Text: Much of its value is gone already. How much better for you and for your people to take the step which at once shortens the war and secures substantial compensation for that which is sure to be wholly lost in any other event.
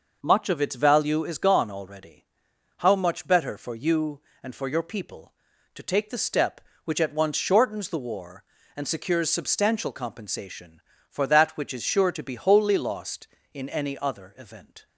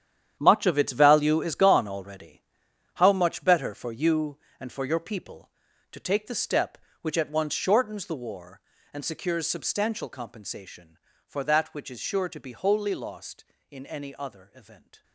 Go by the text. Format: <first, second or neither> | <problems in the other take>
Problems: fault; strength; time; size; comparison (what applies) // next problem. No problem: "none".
first | gets quieter; strong; throughout; 13 dB